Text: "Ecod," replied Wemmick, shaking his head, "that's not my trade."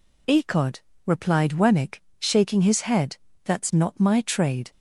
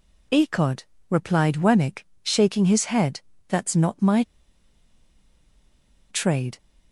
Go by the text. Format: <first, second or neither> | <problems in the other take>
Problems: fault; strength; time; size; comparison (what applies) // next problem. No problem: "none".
first | pauses between "my" and "trade"; strong; at 4.2 s; 1.8 s long